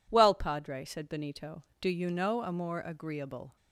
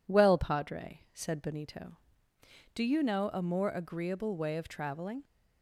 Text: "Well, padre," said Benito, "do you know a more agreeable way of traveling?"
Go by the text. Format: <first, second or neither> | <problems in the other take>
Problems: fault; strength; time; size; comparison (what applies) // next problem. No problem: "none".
second | stops before "way of traveling"; at 3.5 s